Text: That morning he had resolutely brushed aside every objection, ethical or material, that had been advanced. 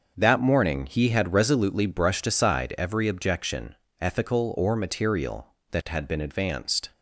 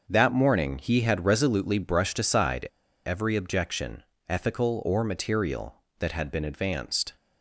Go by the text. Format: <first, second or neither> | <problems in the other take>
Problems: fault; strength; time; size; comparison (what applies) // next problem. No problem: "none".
first | starts louder than the rest; noticeable; until 1.0 s; 6 dB; also in the first // pauses between "aside" and "every"; at 2.6 s; 0.39 s long